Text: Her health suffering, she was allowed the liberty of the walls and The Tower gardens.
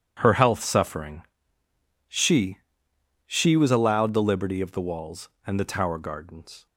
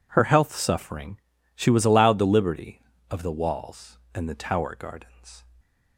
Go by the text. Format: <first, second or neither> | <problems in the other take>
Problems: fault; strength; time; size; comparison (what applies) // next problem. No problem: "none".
second | says "she" twice; at 3.2 s